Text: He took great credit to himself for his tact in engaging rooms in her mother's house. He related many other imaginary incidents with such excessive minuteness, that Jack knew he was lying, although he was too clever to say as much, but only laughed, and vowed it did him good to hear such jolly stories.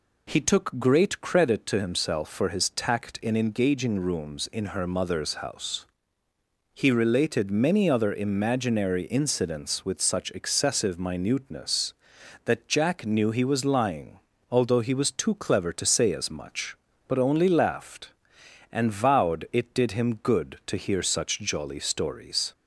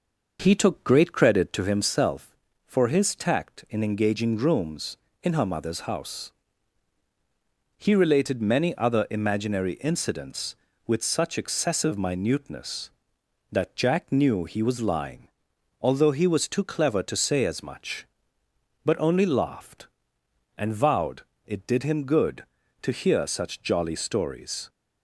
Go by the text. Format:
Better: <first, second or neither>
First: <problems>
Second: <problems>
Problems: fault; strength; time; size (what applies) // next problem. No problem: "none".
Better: first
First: none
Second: starts louder than the rest; noticeable; until 1.9 s; 5.5 dB // pauses between "vowed" and "it"; slight; at 21.2 s; 0.24 s long